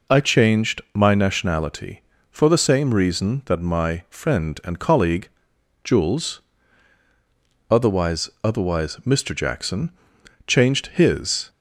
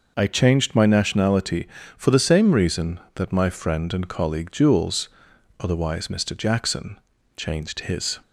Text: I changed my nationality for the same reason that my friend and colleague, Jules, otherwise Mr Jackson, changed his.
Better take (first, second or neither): second